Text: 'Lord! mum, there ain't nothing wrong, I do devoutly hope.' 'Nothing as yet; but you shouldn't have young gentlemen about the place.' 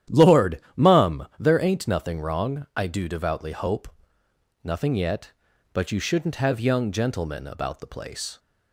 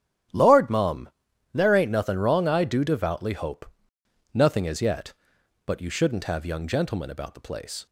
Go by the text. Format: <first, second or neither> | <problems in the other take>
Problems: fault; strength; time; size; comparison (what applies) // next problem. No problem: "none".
second | starts louder than the rest; strong; until 1.2 s; 11 dB; strong in the second // skips "as"; at 4.9 s